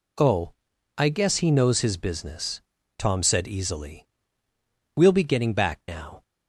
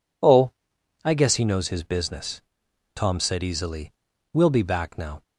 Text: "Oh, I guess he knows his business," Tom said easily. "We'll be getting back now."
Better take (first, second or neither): first